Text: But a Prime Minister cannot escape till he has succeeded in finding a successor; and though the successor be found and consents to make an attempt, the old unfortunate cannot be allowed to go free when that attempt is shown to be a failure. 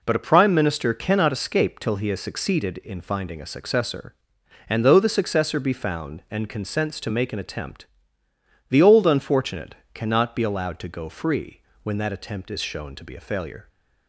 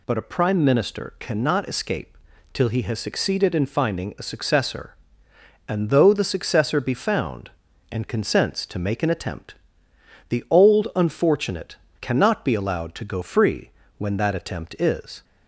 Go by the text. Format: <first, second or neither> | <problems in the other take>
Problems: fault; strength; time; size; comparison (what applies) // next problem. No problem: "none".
first | pauses between "escape" and "till"; slight; at 2.1 s; 0.36 s long // pauses between "unfortunate" and "cannot"; slight; at 11.7 s; 0.24 s long; slight in the first // pauses between "free" and "when"; slight; at 13.7 s; 0.26 s long; slight in the first // stops before "shown to be a failure"; at 15.2 s